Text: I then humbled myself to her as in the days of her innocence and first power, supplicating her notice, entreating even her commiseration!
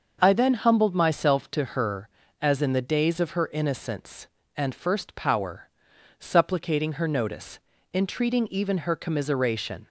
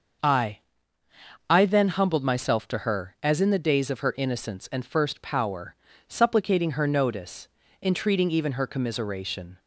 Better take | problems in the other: first | starts louder than the rest; until 2.1 s; 6.5 dB; also in the first // says "I" twice; at 1.4 s

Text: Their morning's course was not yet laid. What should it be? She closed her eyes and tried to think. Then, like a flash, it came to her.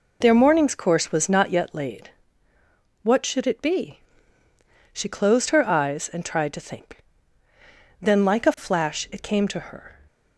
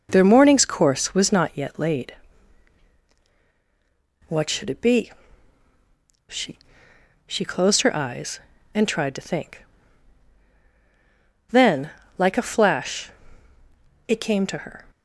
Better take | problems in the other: first | says "She" twice; at 7.2 s

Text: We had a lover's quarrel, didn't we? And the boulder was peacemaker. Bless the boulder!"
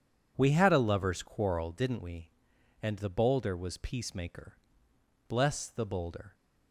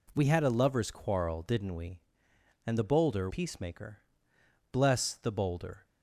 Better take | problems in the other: first | skips "was"; at 3.2 s

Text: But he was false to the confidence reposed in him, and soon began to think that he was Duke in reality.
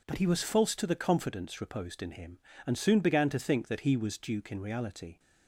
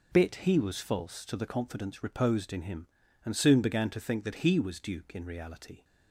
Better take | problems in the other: first | says "Bit" for "But"; at 0.1 s

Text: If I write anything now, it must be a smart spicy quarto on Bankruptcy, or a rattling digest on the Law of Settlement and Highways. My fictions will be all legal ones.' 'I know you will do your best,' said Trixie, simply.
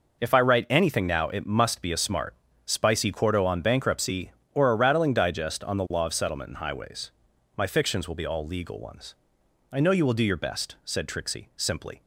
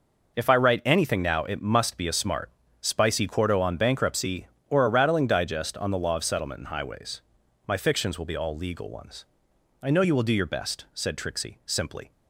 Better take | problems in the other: neither | pauses between "smart" and "spicy"; slight; the same in both

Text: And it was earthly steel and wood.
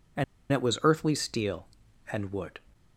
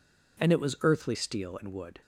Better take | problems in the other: second | pauses between "And" and "it"; slight; at 0.2 s; 0.28 s long

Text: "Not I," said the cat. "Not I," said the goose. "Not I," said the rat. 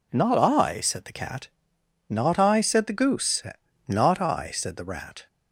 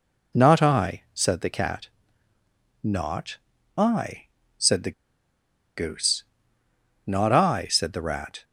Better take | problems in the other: first | pauses between "Not" and "I"; at 3.3 s; 0.40 s long // pauses between "the" and "goose"; noticeable; at 4.9 s; 0.85 s long

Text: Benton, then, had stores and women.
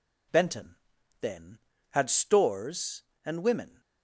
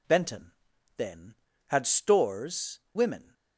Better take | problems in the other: first | skips "and"; at 2.8 s

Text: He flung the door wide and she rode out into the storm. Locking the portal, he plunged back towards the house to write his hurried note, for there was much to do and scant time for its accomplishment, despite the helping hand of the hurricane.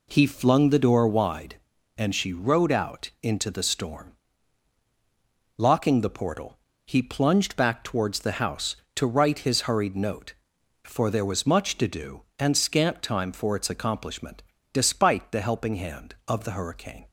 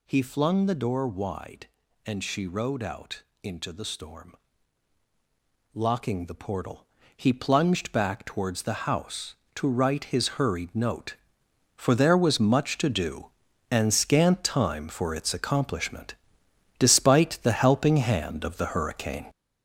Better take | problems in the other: first | gets louder; strong; throughout; 7.5 dB // pauses between "out" and "into"; slight; at 3.2 s; 0.18 s long

